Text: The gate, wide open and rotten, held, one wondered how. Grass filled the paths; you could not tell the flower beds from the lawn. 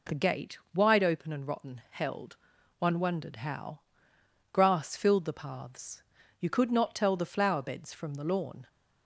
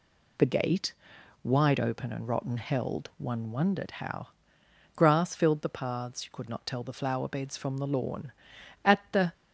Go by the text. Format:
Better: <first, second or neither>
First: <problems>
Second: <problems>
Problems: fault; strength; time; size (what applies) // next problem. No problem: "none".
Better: first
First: none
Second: goes on to say "At the"; slight; from 8.8 s on; 0.48 s long